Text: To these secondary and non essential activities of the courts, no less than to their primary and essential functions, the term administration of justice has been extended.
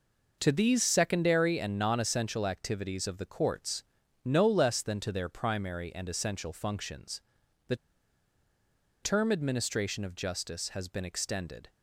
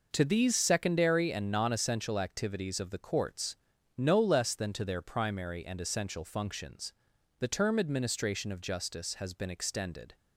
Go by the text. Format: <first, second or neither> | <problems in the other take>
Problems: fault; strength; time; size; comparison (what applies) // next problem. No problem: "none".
second | pauses between "the" and "term"; strong; at 7.7 s; 1.2 s long